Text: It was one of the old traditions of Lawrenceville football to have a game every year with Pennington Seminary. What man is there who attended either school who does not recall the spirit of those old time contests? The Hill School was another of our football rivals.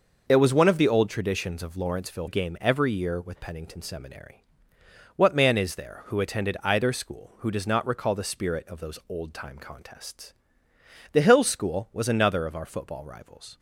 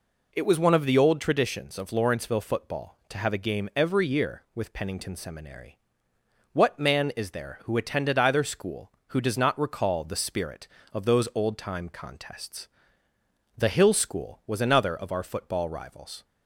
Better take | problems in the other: second | skips "football to have a"; at 2.2 s

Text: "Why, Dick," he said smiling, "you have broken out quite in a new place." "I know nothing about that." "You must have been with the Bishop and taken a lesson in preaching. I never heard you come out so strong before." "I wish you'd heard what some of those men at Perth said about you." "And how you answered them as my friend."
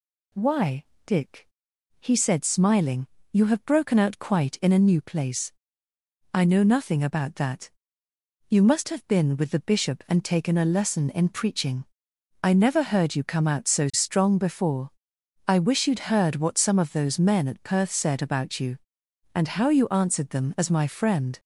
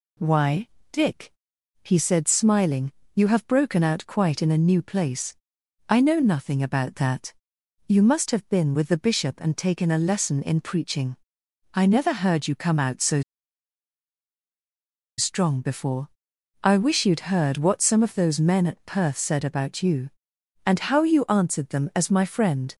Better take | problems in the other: first | pauses between "so" and "strong"; strong; at 13.2 s; 1.9 s long

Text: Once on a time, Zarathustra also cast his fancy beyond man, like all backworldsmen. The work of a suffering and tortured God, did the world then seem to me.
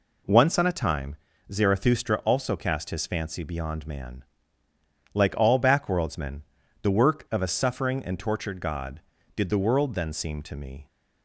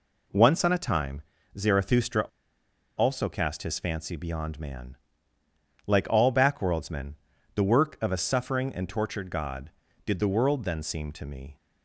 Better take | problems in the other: first | pauses between "Zarathustra" and "also"; noticeable; at 2.2 s; 0.75 s long

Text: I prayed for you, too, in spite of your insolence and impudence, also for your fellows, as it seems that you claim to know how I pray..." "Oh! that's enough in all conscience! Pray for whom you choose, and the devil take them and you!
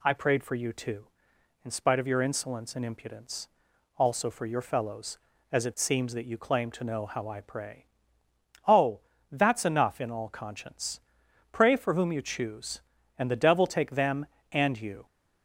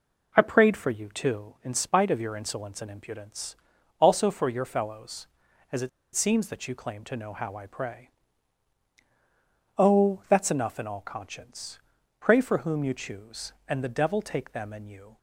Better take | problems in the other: first | pauses between "it" and "seems"; slight; at 5.8 s; 0.26 s long

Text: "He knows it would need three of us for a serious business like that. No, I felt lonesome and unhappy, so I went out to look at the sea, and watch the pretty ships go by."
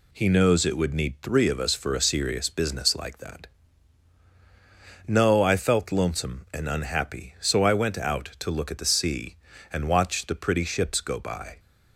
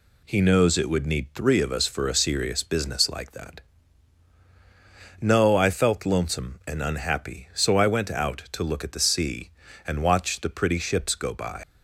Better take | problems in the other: first | leaves "by" unfinished; at 11.6 s; 95 ms

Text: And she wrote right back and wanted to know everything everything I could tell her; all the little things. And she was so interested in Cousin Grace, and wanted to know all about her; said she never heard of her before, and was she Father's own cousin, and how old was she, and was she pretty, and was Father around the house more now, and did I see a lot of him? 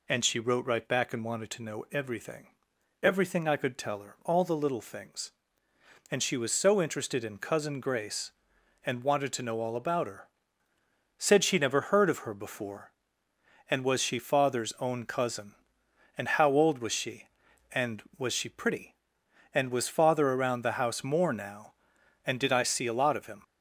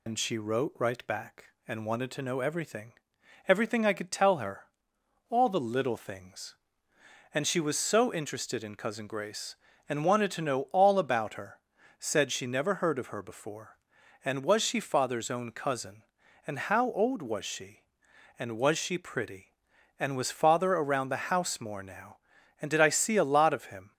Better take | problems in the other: first | loses the start of "And"; at 0.0 s; 105 ms // pauses between "everything" and "everything"; noticeable; at 2.9 s; 0.56 s long; noticeable in the first

